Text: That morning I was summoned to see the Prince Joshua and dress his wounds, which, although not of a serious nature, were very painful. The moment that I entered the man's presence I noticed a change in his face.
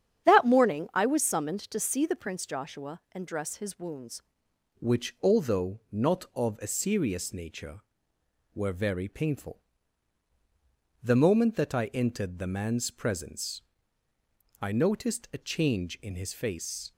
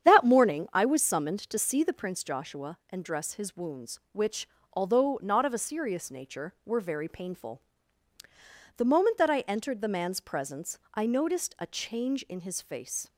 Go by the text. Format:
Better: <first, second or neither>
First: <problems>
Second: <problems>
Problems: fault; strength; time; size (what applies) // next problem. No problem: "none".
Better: second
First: starts louder than the rest; strong; until 1.3 s; 9 dB // changes voice at "which"; from 4.7 s on; 12.2 s long // pauses between "presence" and "I"; noticeable; at 13.6 s; 0.98 s long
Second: starts louder than the rest; strong; until 1.1 s; 8.5 dB // pauses between "presence" and "I"; slight; at 10.7 s; 0.16 s long